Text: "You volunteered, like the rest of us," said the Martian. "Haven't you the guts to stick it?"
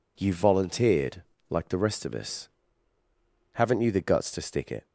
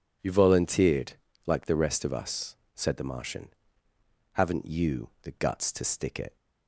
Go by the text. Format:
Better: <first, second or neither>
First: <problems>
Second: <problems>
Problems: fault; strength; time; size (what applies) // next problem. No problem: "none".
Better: second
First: skips "said the Martian"; at 3.0 s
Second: none